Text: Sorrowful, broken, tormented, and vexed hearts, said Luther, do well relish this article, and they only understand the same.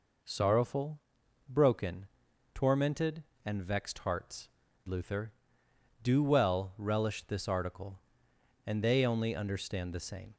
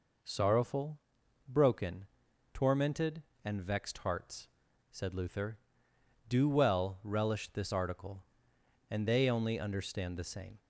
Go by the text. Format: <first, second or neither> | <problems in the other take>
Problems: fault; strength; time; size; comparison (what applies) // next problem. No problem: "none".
second | skips "said"; at 4.6 s